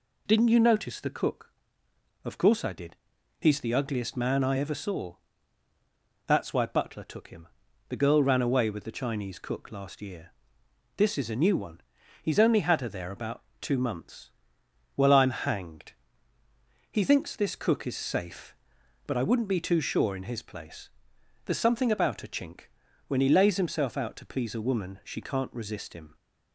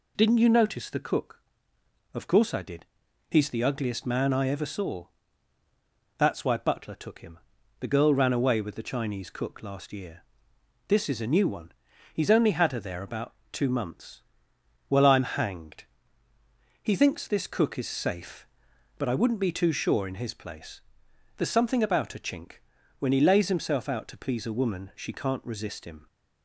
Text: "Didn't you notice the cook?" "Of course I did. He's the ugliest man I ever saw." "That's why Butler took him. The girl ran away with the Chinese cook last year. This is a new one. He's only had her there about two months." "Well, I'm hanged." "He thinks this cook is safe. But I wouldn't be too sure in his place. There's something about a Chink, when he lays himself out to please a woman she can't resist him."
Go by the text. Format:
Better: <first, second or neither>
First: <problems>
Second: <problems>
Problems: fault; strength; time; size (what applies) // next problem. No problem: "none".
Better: neither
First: pauses between "about" and "two"; slight; at 13.4 s; 0.18 s long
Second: pauses between "about" and "two"; slight; at 13.3 s; 0.18 s long